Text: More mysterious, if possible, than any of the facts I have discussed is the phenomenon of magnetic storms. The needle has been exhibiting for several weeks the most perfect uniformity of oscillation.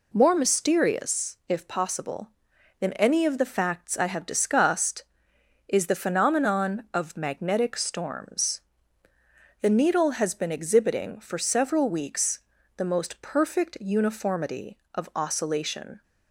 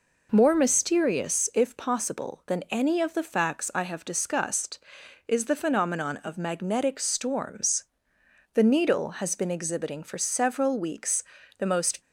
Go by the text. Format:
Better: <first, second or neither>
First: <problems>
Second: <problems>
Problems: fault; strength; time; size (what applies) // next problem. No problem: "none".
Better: first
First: pauses between "weeks" and "the"; slight; at 12.4 s; 0.36 s long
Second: pauses between "weeks" and "the"; slight; at 11.2 s; 0.34 s long // stops before "perfect uniformity of oscillation"; at 12.0 s